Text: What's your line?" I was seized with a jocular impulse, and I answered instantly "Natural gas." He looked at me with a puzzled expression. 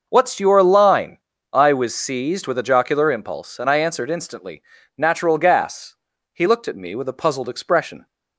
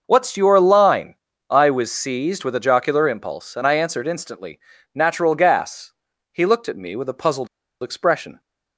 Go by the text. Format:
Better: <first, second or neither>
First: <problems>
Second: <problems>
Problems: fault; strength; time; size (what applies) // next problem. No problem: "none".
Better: first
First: starts louder than the rest; until 1.1 s; 6 dB // pauses between "instantly" and "Natural"; at 4.6 s; 0.38 s long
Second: starts louder than the rest; until 1.0 s; 6 dB // pauses between "instantly" and "Natural"; at 4.5 s; 0.38 s long // pauses between "puzzled" and "expression"; slight; at 7.4 s; 0.34 s long